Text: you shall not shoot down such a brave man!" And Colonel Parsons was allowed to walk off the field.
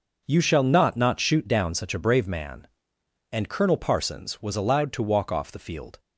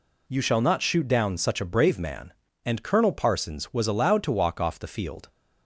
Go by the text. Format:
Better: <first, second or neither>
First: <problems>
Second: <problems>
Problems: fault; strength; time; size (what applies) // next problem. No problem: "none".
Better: second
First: says "not" twice; at 0.9 s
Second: none